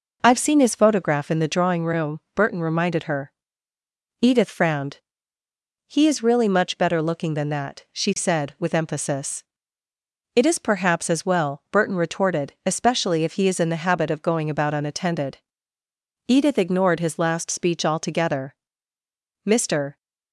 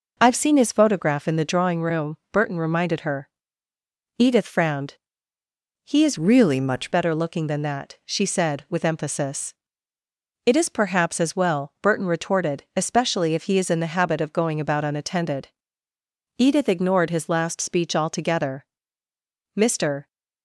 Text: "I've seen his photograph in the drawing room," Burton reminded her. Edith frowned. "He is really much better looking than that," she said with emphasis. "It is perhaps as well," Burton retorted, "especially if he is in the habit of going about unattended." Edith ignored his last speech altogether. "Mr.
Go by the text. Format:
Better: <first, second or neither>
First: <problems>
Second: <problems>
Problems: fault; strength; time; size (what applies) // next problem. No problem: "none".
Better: first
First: none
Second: changes voice from "really" to "much"; from 6.1 to 6.9 s; 0.8 s long